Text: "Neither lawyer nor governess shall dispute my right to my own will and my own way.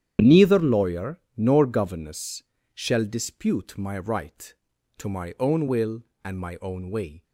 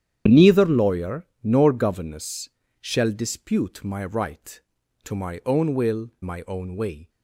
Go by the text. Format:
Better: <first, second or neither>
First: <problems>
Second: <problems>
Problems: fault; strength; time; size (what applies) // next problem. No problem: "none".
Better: first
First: starts louder than the rest; strong; until 1.3 s; 9.5 dB // pauses between "lawyer" and "nor"; slight; at 1.1 s; 0.16 s long // pauses between "governess" and "shall"; slight; at 2.4 s; 0.32 s long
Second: starts louder than the rest; strong; until 1.4 s; 9.5 dB // pauses between "lawyer" and "nor"; slight; at 1.2 s; 0.16 s long // pauses between "governess" and "shall"; slight; at 2.4 s; 0.32 s long // skips "and"; at 6.1 s